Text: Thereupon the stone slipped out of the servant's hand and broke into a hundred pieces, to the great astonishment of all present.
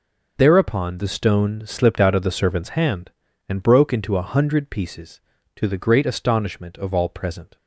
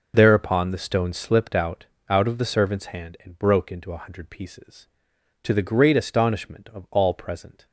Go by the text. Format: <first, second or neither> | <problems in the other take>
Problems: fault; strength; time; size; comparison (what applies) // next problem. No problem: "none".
first | says "out" twice; at 2.0 s